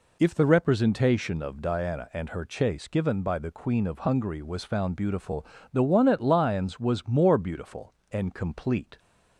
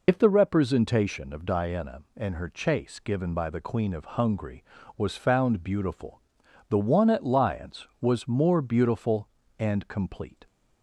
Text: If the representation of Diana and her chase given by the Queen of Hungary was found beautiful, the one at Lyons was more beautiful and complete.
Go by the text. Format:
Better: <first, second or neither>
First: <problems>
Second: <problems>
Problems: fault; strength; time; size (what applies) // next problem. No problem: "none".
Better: first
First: none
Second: loses the start of "If"; at 0.0 s; 80 ms